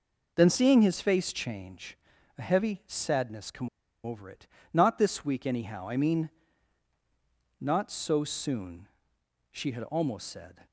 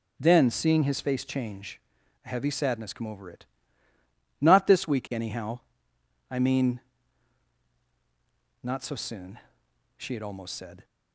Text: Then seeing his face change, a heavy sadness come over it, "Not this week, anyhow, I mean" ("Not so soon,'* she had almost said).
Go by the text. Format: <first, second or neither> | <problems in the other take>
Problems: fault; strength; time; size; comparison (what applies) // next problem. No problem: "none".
second | pauses between "come" and "over"; slight; at 3.6 s; 0.35 s long